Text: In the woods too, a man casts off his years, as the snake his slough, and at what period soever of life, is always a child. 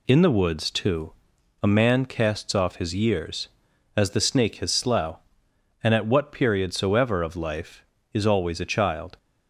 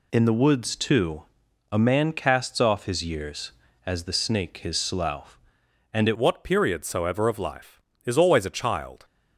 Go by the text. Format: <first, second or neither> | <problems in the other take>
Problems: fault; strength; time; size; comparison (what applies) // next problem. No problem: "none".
first | changes voice at "what"; from 6.1 s on; 2.9 s long